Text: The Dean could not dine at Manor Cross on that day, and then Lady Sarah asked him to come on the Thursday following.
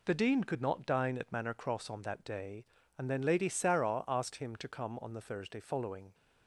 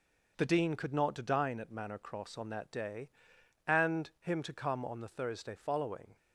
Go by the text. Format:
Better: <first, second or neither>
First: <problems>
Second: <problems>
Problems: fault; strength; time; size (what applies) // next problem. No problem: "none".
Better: first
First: none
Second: skips "then Lady Sarah asked"; at 4.1 s